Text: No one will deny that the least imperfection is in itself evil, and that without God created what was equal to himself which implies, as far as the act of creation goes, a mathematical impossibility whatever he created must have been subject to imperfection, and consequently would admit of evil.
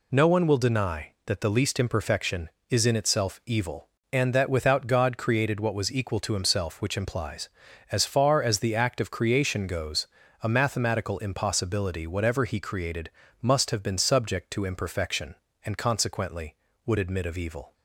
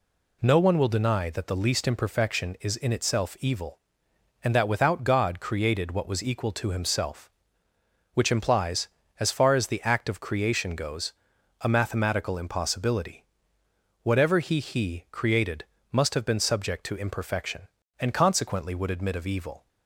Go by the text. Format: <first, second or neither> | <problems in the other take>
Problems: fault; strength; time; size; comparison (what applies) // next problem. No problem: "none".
first | pauses between "impossibility" and "whatever"; noticeable; at 13.2 s; 0.78 s long // says "he" twice; at 14.5 s // pauses between "created" and "must"; slight; at 15.6 s; 0.26 s long; slight in the first